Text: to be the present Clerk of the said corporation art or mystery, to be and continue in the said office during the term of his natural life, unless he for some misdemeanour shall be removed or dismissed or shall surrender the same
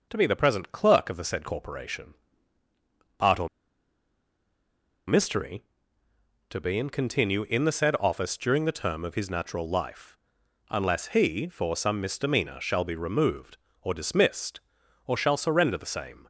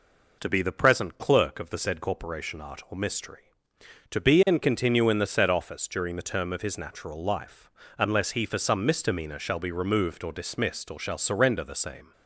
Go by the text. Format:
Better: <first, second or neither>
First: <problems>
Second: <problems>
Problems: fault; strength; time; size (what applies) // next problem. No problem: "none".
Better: second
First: pauses between "corporation" and "art"; at 2.1 s; 1.0 s long // pauses between "or" and "mystery"; strong; at 3.4 s; 1.5 s long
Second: none